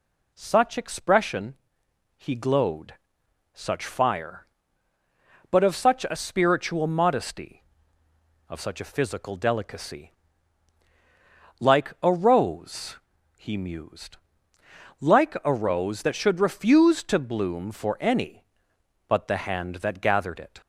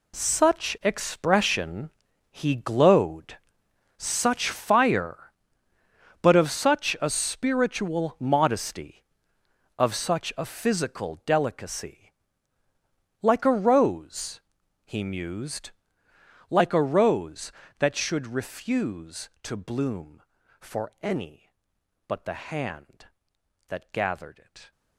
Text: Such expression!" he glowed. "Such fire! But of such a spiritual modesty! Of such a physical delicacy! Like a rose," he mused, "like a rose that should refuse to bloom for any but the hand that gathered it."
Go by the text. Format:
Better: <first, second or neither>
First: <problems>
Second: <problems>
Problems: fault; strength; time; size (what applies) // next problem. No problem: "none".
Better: first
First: none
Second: gets quieter; strong; throughout; 14 dB